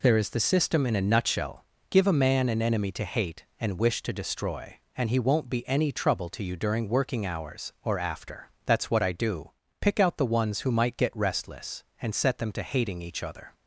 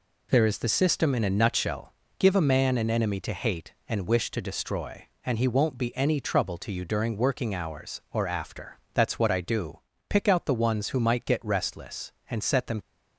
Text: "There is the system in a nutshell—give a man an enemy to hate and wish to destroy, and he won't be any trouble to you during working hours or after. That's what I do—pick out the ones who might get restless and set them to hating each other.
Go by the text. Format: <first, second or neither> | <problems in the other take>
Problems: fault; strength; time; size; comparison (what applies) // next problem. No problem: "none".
first | stops before "to hating each other"; at 12.8 s